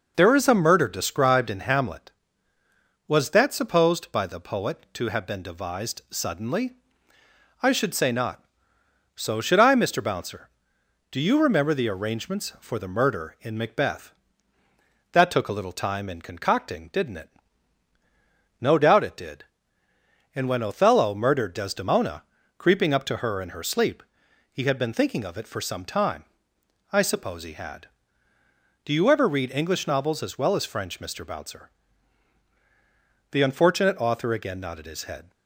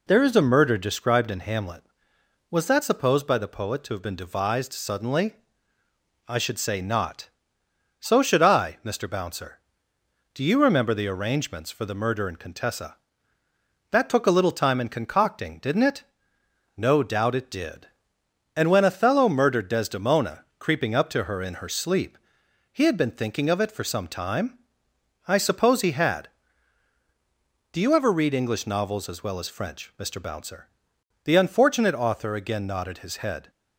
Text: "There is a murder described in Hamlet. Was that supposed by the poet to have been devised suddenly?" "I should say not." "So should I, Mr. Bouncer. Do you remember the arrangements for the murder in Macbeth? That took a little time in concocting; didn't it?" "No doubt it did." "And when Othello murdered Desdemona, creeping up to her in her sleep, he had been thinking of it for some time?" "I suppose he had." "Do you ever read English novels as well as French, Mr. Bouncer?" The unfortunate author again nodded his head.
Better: first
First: none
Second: says "Contessa" for "Macbeth"; at 12.3 s

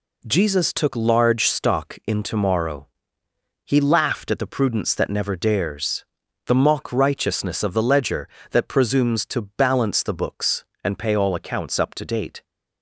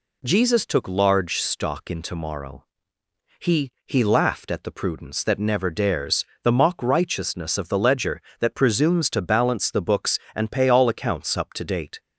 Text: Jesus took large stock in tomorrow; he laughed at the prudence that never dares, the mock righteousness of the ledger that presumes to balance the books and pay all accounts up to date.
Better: first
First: none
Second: says "he" twice; at 3.8 s

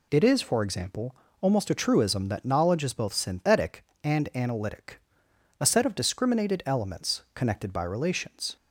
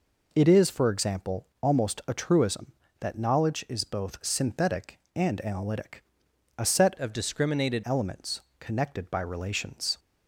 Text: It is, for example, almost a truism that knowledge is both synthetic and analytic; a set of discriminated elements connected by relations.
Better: first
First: none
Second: changes voice from "of" to "discriminated"; from 7.0 to 7.8 s; 0.8 s long // pauses between "elements" and "connected"; slight; at 8.4 s; 0.18 s long

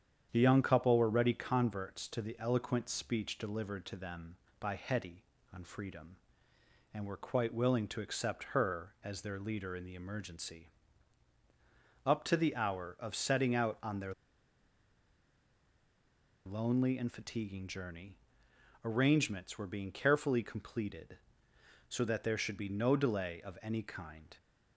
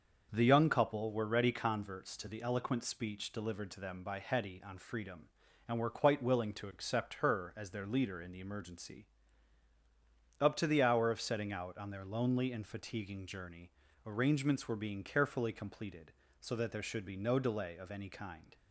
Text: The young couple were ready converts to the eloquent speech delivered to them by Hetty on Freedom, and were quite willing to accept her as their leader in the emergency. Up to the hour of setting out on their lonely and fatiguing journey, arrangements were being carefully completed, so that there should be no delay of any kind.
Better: second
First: starts louder than the rest; strong; until 1.3 s; 8.5 dB // pauses between "their" and "lonely"; strong; at 14.1 s; 2.3 s long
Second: starts louder than the rest; until 1.3 s; 6.5 dB

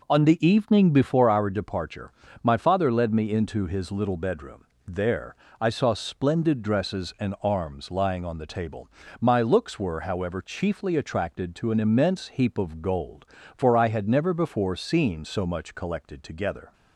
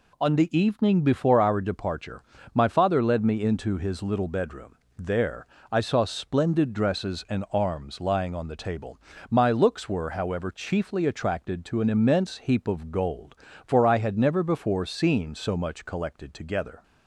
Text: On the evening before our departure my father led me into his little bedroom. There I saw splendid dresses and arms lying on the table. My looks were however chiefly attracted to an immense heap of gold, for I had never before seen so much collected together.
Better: second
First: starts louder than the rest; noticeable; until 1.2 s; 5 dB // pauses between "departure" and "my"; slight; at 2.1 s; 0.32 s long // pauses between "There" and "I"; slight; at 5.3 s; 0.26 s long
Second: pauses between "departure" and "my"; slight; at 2.2 s; 0.32 s long // pauses between "There" and "I"; slight; at 5.4 s; 0.26 s long

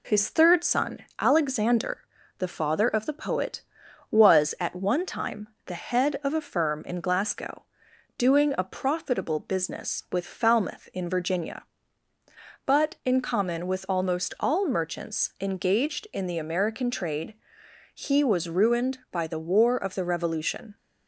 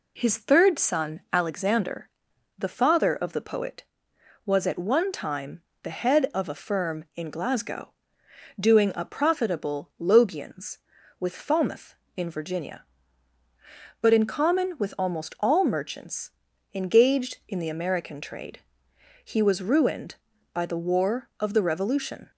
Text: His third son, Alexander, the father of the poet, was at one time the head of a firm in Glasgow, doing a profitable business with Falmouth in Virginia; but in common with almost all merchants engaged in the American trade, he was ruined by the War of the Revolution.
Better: first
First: pauses between "time" and "the"; slight; at 5.4 s; 0.18 s long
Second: pauses between "time" and "the"; slight; at 5.6 s; 0.22 s long // says "logians" for "business"; at 10.0 s // pauses between "merchants" and "engaged"; at 16.3 s; 0.42 s long

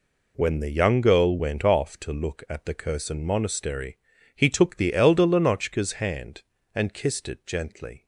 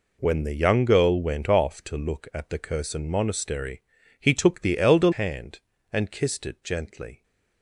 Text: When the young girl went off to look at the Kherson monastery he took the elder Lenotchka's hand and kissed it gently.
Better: first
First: pauses between "monastery" and "he"; at 3.9 s; 0.40 s long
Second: pauses between "monastery" and "he"; at 3.7 s; 0.40 s long // skips "Lenotchka's"; at 5.1 s

